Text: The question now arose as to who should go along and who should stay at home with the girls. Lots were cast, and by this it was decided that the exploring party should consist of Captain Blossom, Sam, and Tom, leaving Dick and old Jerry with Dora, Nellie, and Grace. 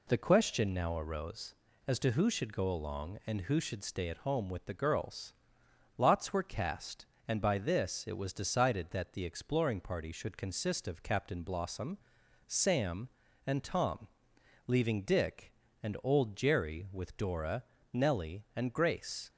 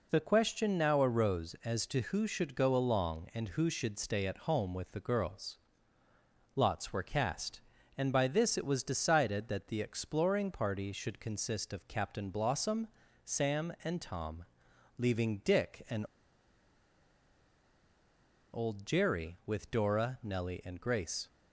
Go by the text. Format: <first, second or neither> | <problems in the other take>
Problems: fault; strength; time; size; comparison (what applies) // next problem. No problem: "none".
first | pauses between "and" and "old"; strong; at 16.0 s; 2.4 s long